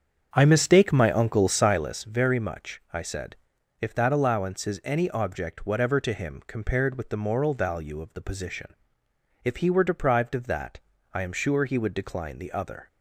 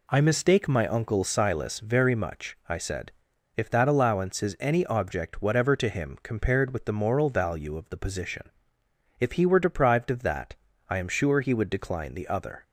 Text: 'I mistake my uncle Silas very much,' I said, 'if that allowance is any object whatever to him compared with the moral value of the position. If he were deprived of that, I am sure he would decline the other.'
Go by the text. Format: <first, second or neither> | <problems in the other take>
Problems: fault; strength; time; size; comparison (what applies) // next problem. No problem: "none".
second | starts louder than the rest; strong; until 1.9 s; 7.5 dB